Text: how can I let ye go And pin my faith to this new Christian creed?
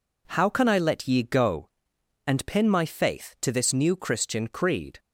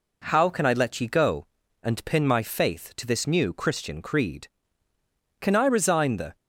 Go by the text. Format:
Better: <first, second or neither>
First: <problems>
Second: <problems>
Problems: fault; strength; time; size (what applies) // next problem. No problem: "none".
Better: first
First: none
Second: goes on to say "Can I resign the"; noticeable; from 5.4 s on; 0.94 s long